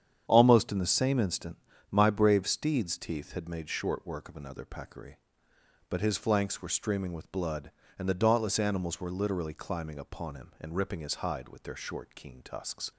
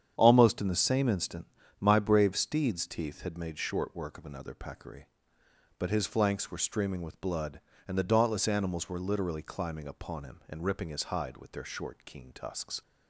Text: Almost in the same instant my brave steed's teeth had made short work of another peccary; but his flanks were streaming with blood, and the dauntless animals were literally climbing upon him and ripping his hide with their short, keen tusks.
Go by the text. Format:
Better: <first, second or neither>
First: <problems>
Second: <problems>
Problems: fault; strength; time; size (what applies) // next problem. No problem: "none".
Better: neither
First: starts louder than the rest; strong; until 1.2 s; 8.5 dB // pauses between "instant" and "my"; slight; at 1.5 s; 0.32 s long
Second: starts louder than the rest; strong; until 1.1 s; 8.5 dB // pauses between "instant" and "my"; slight; at 1.4 s; 0.32 s long